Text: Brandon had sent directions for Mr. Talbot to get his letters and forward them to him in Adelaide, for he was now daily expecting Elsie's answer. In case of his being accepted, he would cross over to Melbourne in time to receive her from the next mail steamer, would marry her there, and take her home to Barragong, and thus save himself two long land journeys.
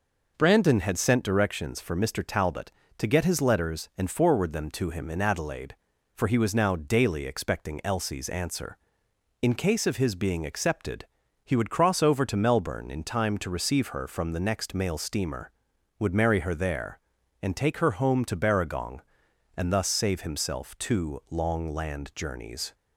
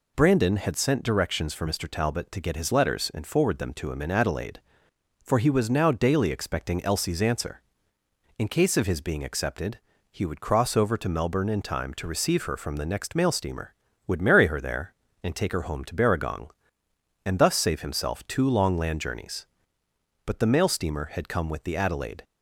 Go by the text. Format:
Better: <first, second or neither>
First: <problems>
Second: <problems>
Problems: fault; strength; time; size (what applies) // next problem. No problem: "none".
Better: first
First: none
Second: goes on to say "But the mail steamer had come with the Adelaide"; strong; from 20.2 s on; 1.9 s long